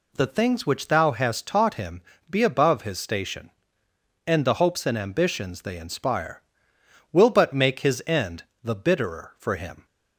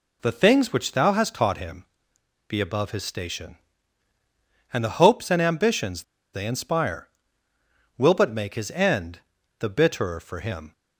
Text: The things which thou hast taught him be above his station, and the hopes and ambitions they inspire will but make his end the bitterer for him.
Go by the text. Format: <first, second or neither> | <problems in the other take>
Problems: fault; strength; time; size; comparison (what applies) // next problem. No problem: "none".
first | pauses between "him" and "be"; noticeable; at 1.8 s; 0.64 s long; slight in the first // pauses between "ambitions" and "they"; slight; at 6.0 s; 0.31 s long // pauses between "end" and "the"; at 9.2 s; 0.38 s long; slight in the first